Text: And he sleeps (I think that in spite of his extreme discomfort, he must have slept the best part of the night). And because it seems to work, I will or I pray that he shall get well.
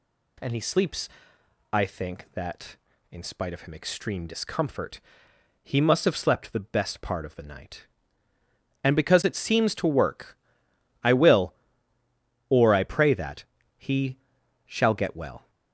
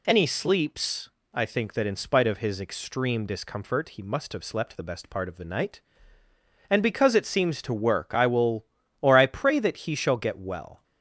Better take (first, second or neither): second